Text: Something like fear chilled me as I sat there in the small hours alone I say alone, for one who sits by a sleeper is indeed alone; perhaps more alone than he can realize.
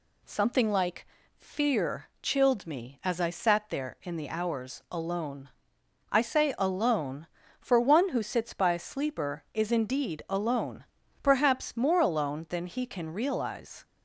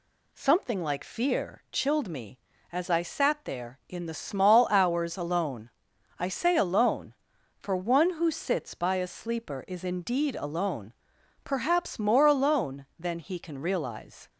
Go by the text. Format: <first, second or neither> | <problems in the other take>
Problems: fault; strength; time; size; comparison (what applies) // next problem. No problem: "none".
second | pauses between "like" and "fear"; slight; at 1.0 s; 0.30 s long // skips "small"; at 4.2 s // pauses between "alone" and "I"; noticeable; at 5.4 s; 0.64 s long; noticeable in the second